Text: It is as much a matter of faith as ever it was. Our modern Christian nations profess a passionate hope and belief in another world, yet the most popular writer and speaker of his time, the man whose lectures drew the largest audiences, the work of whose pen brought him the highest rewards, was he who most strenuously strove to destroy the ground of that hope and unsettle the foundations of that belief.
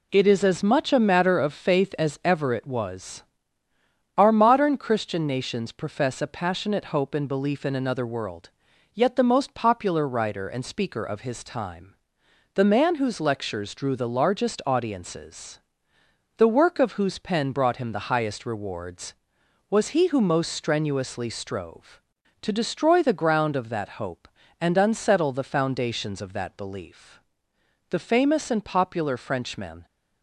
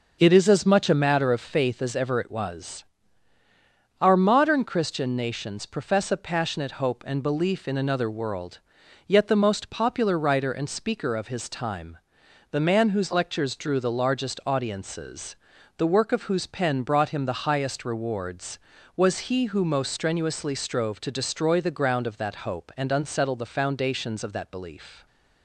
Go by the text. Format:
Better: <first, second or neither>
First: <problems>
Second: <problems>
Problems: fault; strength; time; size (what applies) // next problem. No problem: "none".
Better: second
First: goes on to say "The famous and popular Frenchman"; strong; from 27.9 s on; 1.9 s long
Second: none